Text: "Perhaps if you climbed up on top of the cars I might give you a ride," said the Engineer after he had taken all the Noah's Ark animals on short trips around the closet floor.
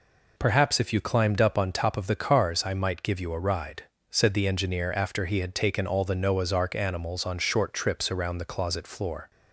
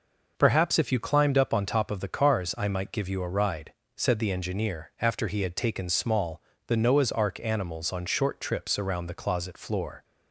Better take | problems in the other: first | says "small" for "all"; at 5.8 s

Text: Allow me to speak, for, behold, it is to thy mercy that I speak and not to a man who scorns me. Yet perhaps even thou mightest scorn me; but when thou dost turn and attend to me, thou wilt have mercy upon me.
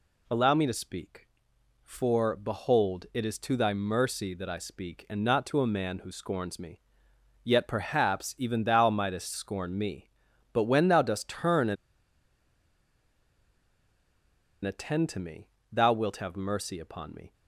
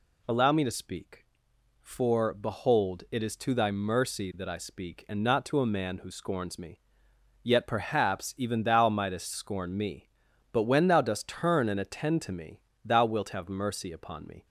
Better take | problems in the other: second | pauses between "and" and "attend"; strong; at 11.7 s; 2.8 s long

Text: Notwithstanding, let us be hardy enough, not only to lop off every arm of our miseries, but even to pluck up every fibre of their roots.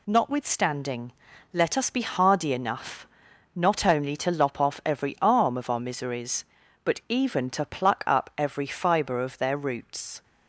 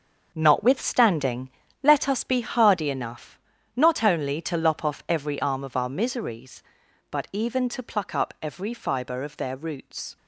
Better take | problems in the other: first | gets quieter; strong; throughout; 10 dB

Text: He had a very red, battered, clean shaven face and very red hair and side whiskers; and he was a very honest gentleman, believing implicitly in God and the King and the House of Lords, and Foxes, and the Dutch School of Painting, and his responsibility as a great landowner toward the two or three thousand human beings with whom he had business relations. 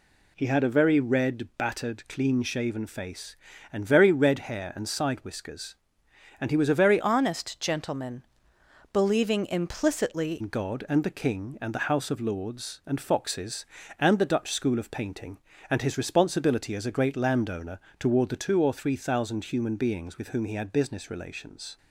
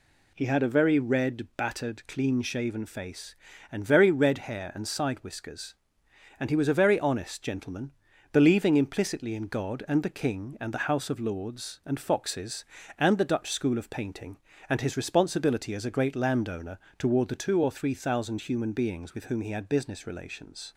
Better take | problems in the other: second | changes voice from "honest" to "implicitly"; from 7.0 to 10.4 s; 3.4 s long // pauses between "landowner" and "toward"; slight; at 17.8 s; 0.18 s long; slight in the second

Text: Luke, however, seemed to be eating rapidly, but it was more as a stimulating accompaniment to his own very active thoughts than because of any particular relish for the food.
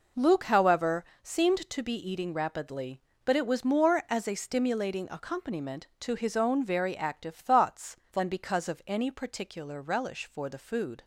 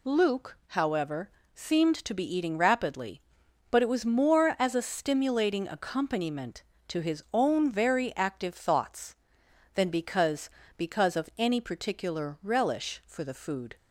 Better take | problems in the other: first | says "because" twice; at 10.7 s

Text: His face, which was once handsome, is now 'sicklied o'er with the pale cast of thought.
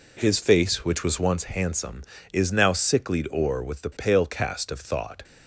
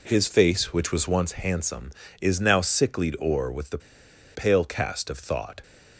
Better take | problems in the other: first | pauses between "the" and "pale"; noticeable; at 3.7 s; 0.56 s long

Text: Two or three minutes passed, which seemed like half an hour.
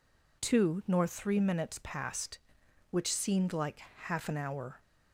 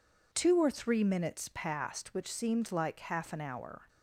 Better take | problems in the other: second | says "nor" for "or"; at 0.8 s

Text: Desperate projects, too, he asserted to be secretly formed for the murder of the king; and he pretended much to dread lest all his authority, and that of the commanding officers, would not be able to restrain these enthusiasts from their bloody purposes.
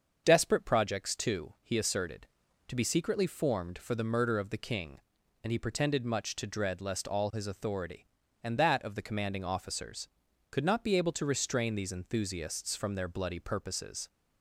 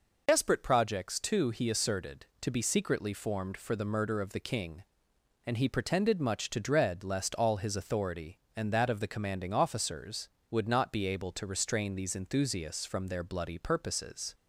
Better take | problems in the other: second | starts louder than the rest; until 1.2 s; 6.5 dB // says "could" for "would"; at 10.5 s

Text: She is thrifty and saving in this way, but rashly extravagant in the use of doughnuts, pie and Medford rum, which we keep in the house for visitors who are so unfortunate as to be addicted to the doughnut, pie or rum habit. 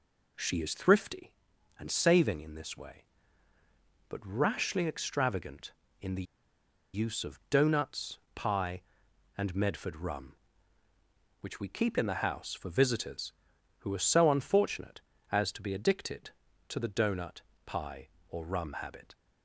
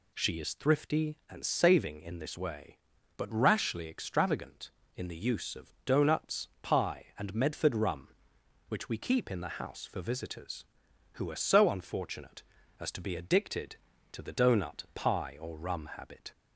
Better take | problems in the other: second | pauses between "the" and "use"; noticeable; at 6.2 s; 0.70 s long

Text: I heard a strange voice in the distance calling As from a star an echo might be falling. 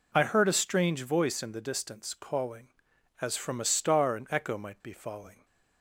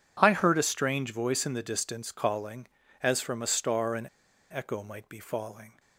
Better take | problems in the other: first | pauses between "an" and "echo"; at 4.0 s; 0.43 s long

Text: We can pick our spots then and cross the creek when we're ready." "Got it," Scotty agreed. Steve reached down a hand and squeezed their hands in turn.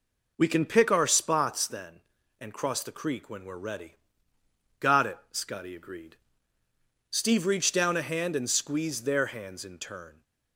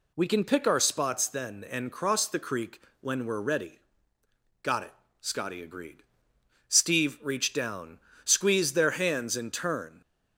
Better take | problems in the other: first | pauses between "creek" and "when"; slight; at 2.8 s; 0.18 s long // skips "a hand and"; at 8.1 s

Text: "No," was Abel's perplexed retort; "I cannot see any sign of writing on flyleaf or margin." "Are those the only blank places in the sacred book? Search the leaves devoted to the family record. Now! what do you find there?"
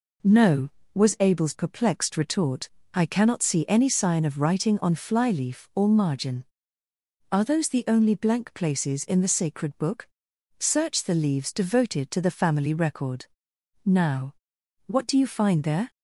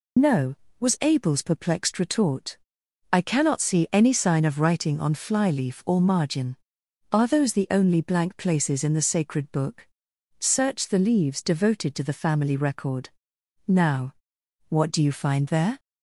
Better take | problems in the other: first | loses the start of "No"; at 0.1 s; 55 ms

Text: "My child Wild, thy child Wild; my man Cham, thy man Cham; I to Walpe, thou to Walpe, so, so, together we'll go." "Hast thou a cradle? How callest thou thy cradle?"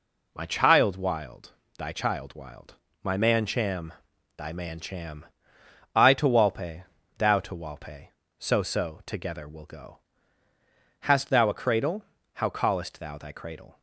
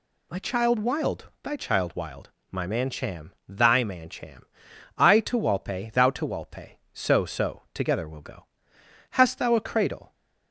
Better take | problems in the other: first | stops before "How callest thou thy cradle"; at 10.1 s

